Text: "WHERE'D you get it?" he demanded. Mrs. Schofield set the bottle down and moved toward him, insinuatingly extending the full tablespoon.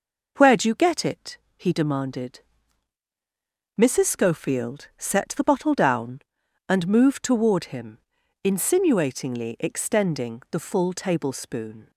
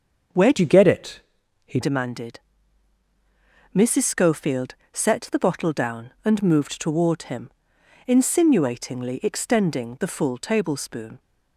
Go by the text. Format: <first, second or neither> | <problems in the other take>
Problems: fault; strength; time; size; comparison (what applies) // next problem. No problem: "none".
first | starts louder than the rest; until 1.7 s; 6.5 dB // changes voice from "you" to "he"; from 0.5 to 1.7 s; 1.2 s long // pauses between "Schofield" and "set"; slight; at 4.7 s; 0.20 s long